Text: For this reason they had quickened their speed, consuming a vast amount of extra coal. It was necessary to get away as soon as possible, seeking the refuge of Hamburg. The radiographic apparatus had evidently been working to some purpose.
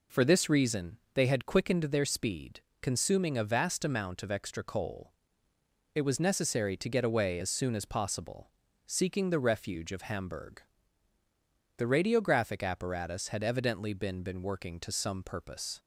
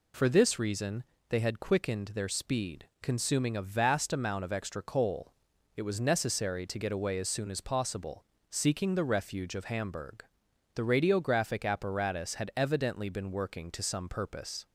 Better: second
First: pauses between "reason" and "they"; slight; at 0.9 s; 0.16 s long // says "been" twice; at 14.2 s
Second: pauses between "reason" and "they"; slight; at 1.0 s; 0.26 s long

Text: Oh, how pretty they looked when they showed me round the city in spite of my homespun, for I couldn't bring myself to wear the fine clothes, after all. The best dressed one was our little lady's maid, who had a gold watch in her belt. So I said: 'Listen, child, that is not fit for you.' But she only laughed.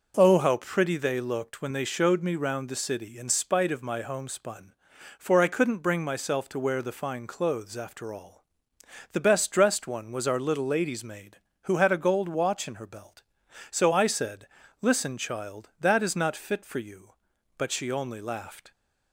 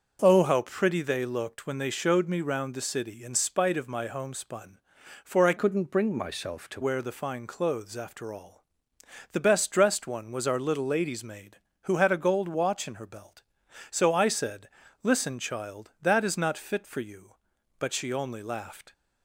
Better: first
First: none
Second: starts louder than the rest; until 1.2 s; 6.5 dB // changes voice from "couldn't" to "to"; from 5.5 to 6.8 s; 1.3 s long

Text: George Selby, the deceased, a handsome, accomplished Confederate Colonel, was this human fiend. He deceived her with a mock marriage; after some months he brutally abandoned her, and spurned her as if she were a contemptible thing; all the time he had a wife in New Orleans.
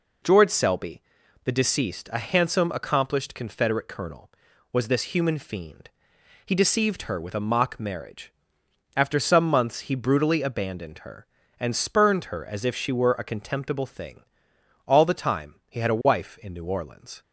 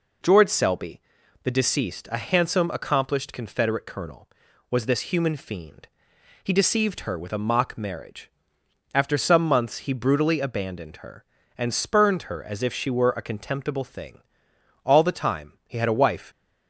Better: first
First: none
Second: stops before "in New Orleans"; at 16.3 s

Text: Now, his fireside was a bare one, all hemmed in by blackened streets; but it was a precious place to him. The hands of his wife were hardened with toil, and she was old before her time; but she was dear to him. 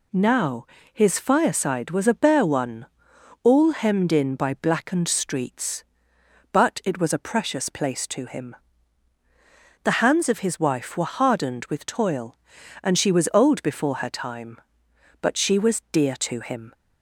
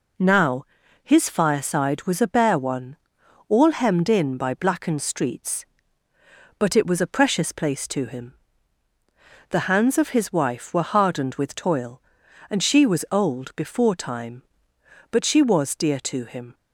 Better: first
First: none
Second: skips "her"; at 13.9 s

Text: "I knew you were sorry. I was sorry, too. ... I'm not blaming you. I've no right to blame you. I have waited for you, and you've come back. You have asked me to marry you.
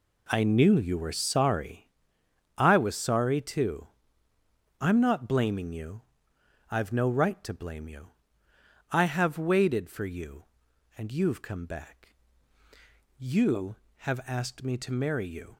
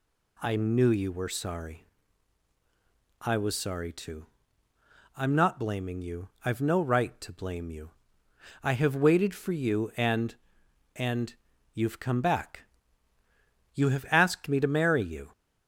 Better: first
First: none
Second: says "and" twice; at 10.9 s

